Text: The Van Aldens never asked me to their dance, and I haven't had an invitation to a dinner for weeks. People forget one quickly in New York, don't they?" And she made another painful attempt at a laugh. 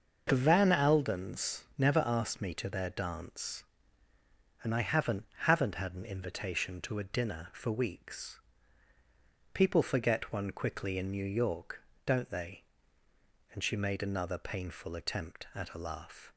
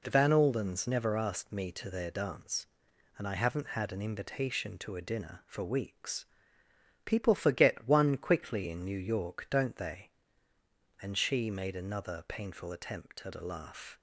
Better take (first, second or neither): second